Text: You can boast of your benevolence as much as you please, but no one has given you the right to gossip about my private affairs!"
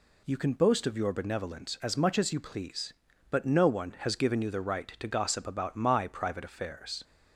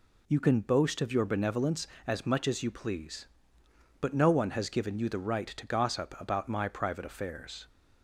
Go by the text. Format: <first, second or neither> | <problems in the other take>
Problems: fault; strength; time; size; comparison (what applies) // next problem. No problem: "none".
neither | none